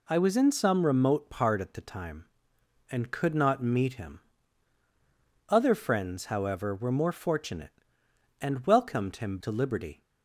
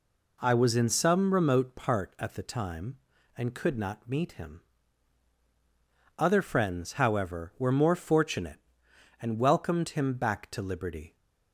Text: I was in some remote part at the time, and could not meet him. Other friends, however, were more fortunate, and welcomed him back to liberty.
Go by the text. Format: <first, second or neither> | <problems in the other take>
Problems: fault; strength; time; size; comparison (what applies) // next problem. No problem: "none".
second | skips "back"; at 9.3 s